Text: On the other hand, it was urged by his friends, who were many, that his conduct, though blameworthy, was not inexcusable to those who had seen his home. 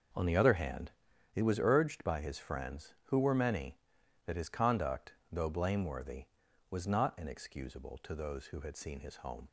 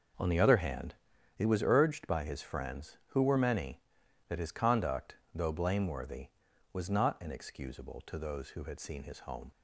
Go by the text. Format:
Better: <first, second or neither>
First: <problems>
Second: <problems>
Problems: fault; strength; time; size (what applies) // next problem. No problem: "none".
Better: neither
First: none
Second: none